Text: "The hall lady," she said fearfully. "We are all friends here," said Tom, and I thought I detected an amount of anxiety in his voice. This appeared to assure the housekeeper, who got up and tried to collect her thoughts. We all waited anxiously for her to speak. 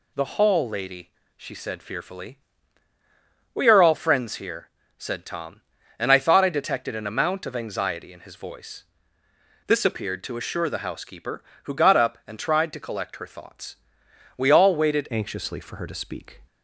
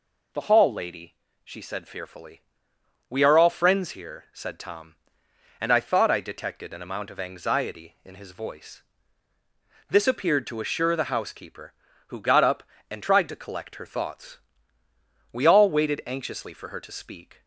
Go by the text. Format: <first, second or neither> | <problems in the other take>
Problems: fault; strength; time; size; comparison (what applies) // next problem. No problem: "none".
second | changes voice at "anxiously"; from 15.0 s on; 1.4 s long